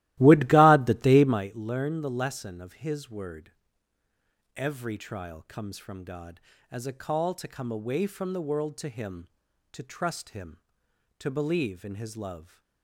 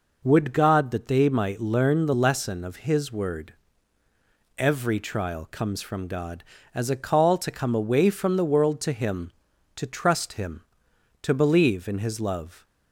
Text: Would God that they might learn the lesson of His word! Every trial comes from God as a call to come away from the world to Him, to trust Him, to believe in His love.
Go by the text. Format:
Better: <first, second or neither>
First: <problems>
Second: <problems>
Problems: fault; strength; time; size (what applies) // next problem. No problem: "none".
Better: second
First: starts louder than the rest; strong; until 1.5 s; 16.5 dB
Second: none